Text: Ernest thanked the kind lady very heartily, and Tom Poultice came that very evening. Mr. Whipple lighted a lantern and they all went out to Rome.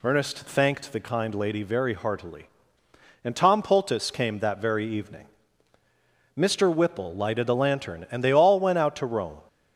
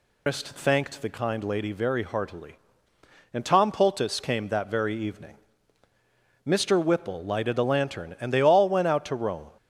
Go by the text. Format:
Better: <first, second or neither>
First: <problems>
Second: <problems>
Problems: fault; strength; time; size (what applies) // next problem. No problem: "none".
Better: first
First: none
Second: loses the start of "Ernest"; at 0.2 s; 145 ms